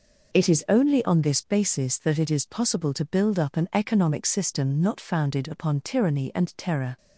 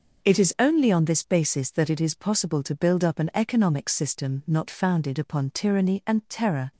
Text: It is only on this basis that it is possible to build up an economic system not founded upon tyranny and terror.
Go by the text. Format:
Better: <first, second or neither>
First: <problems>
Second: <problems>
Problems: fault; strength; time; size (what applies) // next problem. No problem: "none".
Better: neither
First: none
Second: none